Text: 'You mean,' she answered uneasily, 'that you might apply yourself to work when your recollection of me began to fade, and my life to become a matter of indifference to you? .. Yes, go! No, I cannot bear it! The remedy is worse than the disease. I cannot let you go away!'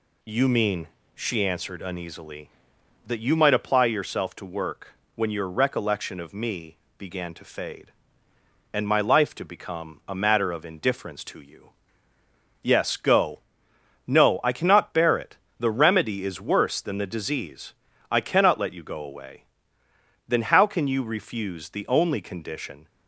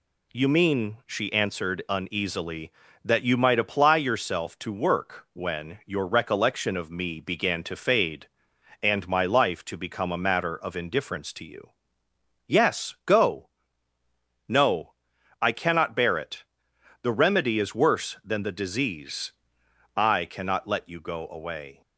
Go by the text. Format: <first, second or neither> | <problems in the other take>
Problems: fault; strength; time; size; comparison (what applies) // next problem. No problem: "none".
second | pauses between "work" and "when"; slight; at 4.9 s; 0.22 s long // pauses between "me" and "began"; slight; at 6.7 s; 0.22 s long // goes on to say "Then how can you refuse the only condition"; strong; from 20.2 s on; 2.6 s long